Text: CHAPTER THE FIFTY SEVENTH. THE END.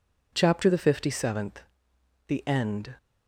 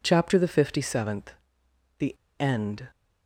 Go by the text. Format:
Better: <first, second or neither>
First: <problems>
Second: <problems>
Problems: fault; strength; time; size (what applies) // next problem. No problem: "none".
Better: first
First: none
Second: pauses between "THE" and "END"; slight; at 2.1 s; 0.22 s long